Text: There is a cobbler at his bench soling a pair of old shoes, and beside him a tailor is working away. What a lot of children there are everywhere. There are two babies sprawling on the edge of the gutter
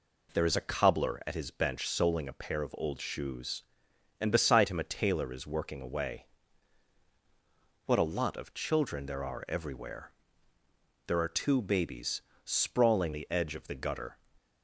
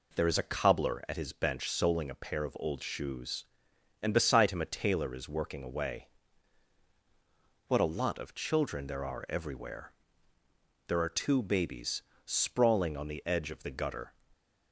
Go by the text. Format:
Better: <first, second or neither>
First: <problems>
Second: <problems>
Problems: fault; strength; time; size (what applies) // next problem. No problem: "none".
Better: second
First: pauses between "babies" and "sprawling"; slight; at 12.2 s; 0.22 s long // skips "on"; at 13.1 s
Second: pauses between "babies" and "sprawling"; slight; at 12.0 s; 0.22 s long